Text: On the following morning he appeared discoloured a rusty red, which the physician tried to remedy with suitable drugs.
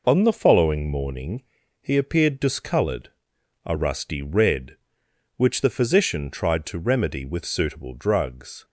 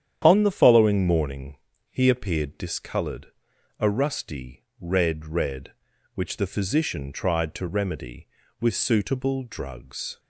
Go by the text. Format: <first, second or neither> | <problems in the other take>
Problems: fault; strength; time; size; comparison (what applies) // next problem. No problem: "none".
first | starts louder than the rest; strong; until 1.2 s; 9.5 dB // pauses between "morning" and "he"; slight; at 1.5 s; 0.34 s long; also in the first // pauses between "discoloured" and "a"; noticeable; at 3.2 s; 0.52 s long; noticeable in the first // pauses between "rusty" and "red"; slight; at 4.6 s; 0.16 s long // says "red" twice; at 5.2 s